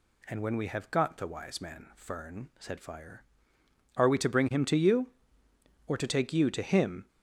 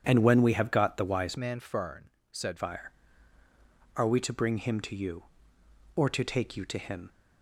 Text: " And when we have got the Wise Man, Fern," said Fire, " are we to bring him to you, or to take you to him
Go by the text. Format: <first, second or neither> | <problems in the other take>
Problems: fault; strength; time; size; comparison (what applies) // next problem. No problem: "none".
first | starts louder than the rest; strong; until 1.0 s; 7 dB // changes voice from "Man" to "said"; from 1.3 to 2.5 s; 1.2 s long